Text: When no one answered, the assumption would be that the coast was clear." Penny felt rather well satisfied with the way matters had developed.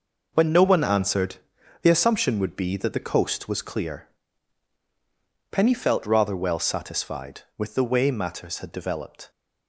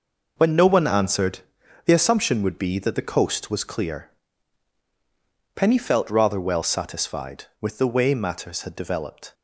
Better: neither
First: none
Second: none

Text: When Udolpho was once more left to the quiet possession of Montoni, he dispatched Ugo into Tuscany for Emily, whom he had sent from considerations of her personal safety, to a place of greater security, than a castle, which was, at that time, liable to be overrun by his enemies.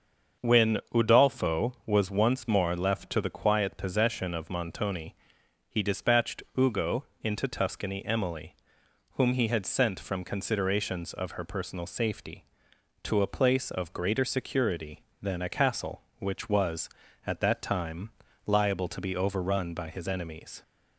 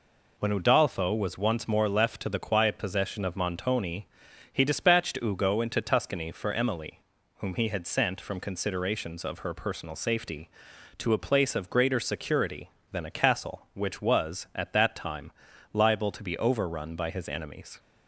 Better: second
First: starts louder than the rest; until 1.5 s; 6.5 dB // pauses between "When" and "Udolpho"; slight; at 0.7 s; 0.16 s long // pauses between "Ugo" and "into"; slight; at 7.0 s; 0.18 s long // skips "for"; at 8.0 s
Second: none

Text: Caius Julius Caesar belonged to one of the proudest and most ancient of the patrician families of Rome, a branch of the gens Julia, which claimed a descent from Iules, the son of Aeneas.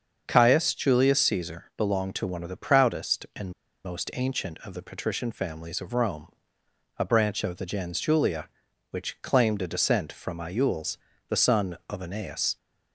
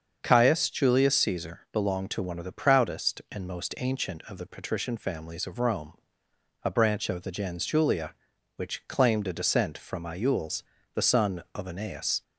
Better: second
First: starts louder than the rest; until 1.3 s; 7 dB // pauses between "and" and "most"; slight; at 3.5 s; 0.33 s long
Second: starts louder than the rest; until 1.2 s; 7 dB

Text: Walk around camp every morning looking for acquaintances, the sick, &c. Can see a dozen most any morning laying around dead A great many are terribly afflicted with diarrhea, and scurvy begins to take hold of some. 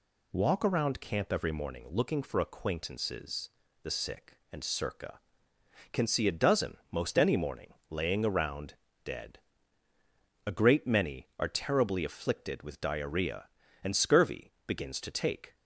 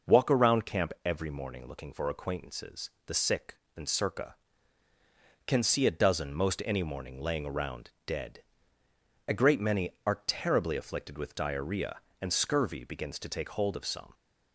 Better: second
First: pauses between "morning" and "laying"; slight; at 7.7 s; 0.16 s long // pauses between "around" and "dead"; slight; at 8.7 s; 0.28 s long // pauses between "dead" and "A"; at 9.3 s; 1.0 s long // stops before "hold of some"; at 15.5 s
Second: pauses between "dead" and "A"; noticeable; at 8.4 s; 0.86 s long

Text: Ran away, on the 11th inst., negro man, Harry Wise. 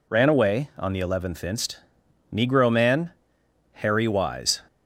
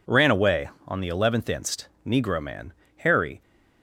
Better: first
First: none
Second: stops before "Wise"; at 3.4 s

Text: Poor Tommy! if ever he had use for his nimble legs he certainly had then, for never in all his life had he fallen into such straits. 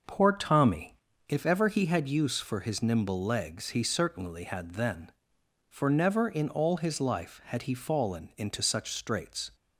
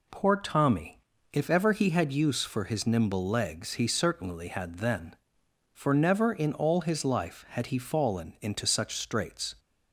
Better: second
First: starts louder than the rest; noticeable; until 1.1 s; 6 dB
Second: none

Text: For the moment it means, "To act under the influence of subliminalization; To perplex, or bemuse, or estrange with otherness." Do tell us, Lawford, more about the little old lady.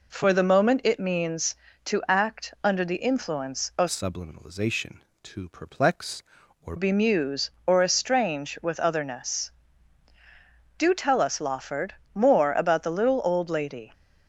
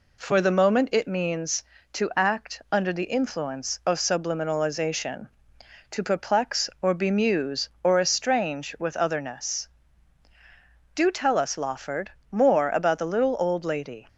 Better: second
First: changes voice from "subliminalization" to "or"; from 3.8 to 6.7 s; 2.9 s long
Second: none

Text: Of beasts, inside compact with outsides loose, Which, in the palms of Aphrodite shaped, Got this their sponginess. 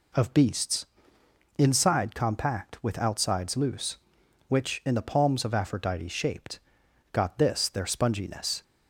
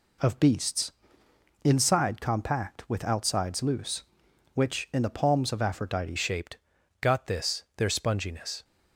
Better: first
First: none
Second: changes voice at "shaped"; from 6.1 s on; 2.5 s long

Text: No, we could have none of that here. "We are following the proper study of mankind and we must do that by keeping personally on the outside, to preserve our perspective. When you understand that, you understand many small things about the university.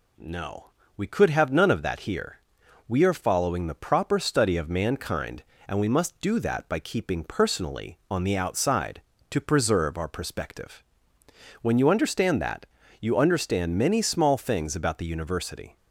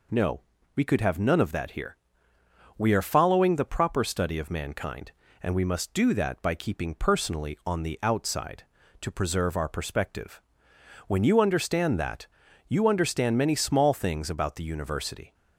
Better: neither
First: none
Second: none

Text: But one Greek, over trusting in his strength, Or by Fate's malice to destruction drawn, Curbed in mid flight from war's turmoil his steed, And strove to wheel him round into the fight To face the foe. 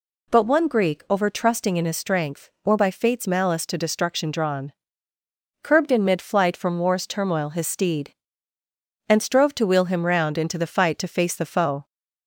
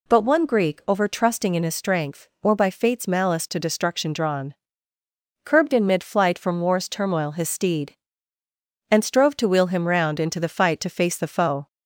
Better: neither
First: none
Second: none

